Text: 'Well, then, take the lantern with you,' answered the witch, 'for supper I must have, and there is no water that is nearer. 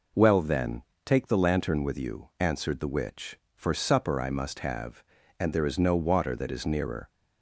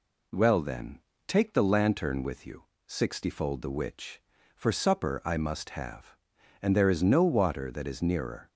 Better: first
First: none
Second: says "sixtyfold" for "answered"; at 2.8 s

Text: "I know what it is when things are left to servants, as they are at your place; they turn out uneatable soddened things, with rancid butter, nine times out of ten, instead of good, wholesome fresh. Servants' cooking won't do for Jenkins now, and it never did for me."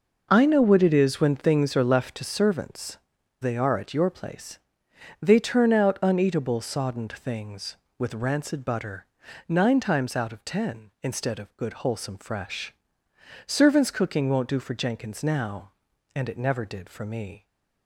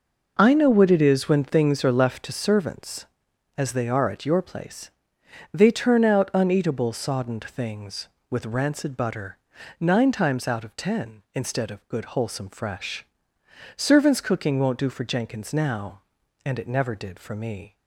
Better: second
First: skips "as"; at 3.1 s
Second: none

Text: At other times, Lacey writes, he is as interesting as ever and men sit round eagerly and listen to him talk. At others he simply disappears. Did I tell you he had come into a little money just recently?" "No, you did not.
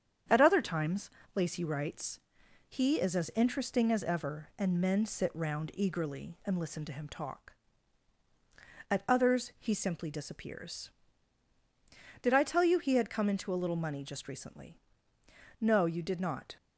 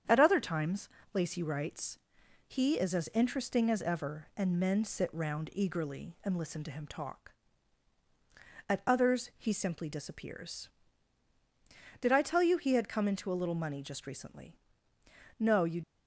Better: first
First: starts louder than the rest; strong; until 1.5 s; 8.5 dB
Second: starts louder than the rest; strong; until 1.3 s; 8.5 dB // stops before "did not"; at 15.8 s

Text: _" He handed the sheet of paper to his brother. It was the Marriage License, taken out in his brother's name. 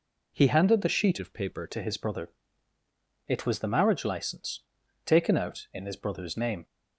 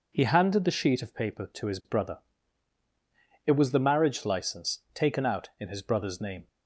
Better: second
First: changes voice from "of" to "paper"; from 1.1 to 1.6 s; 0.5 s long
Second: none

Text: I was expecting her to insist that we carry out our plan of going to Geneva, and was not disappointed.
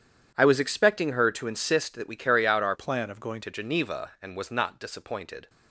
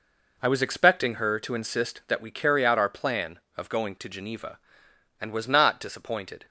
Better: second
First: starts louder than the rest; strong; until 1.3 s; 9.5 dB // changes voice from "plan" to "going"; from 2.7 to 3.4 s; 0.7 s long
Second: none

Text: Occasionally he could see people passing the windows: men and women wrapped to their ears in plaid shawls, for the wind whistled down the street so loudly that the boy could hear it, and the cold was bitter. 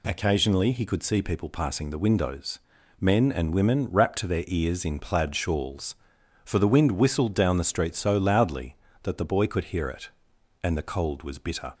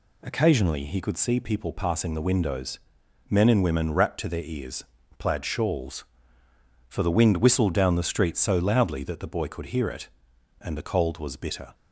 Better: first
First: none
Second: skips "in"; at 5.0 s

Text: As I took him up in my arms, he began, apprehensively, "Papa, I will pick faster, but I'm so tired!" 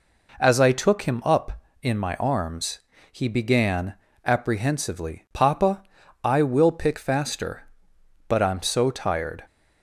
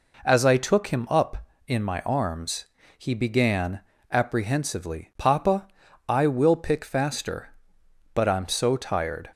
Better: neither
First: none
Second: none

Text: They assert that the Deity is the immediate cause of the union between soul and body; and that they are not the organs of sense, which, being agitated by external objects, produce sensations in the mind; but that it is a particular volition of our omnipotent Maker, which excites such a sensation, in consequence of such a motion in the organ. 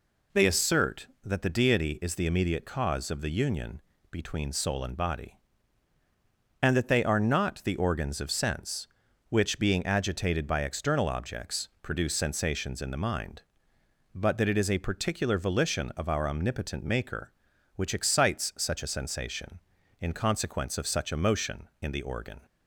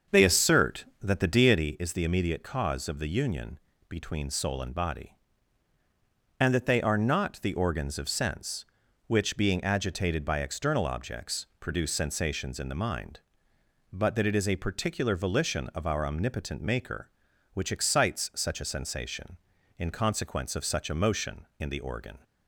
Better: first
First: pauses between "union" and "between"; slight; at 3.8 s; 0.32 s long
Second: starts louder than the rest; until 1.7 s; 7 dB // pauses between "union" and "between"; slight; at 3.5 s; 0.32 s long

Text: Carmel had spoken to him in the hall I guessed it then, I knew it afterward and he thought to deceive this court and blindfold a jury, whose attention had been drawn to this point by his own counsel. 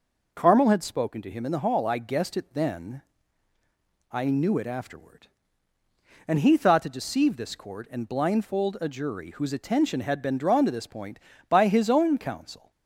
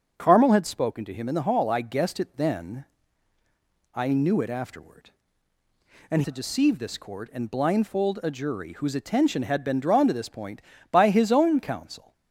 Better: first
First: none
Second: starts louder than the rest; until 1.1 s; 6.5 dB // skips "he thought"; at 6.2 s

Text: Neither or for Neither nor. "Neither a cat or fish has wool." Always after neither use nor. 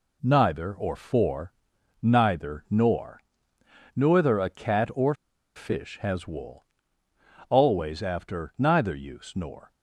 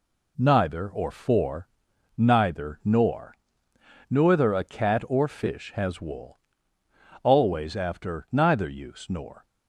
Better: second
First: pauses between "for" and "Neither"; noticeable; at 1.5 s; 0.52 s long // pauses between "or" and "fish"; at 5.1 s; 0.40 s long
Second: pauses between "for" and "Neither"; noticeable; at 1.6 s; 0.52 s long

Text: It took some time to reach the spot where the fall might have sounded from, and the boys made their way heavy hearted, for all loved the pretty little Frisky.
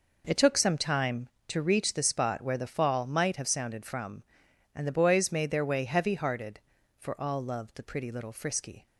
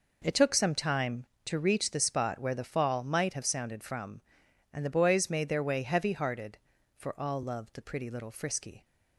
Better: neither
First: none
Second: none

